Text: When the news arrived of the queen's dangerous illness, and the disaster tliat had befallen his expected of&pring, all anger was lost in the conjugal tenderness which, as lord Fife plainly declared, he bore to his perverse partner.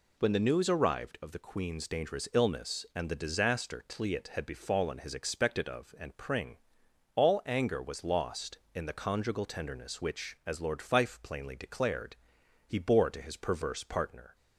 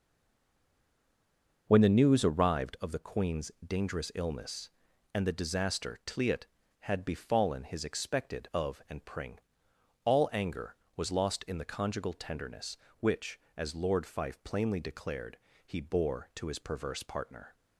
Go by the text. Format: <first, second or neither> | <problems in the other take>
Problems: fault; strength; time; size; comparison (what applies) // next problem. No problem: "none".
first | stays silent before the first word; noticeable; until 1.6 s; 1.6 s long